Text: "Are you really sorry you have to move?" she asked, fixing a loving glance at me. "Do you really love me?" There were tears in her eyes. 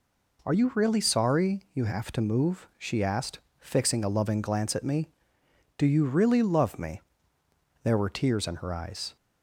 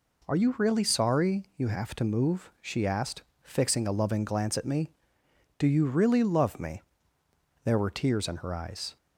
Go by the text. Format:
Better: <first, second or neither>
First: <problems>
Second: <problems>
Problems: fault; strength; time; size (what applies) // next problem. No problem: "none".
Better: neither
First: none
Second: none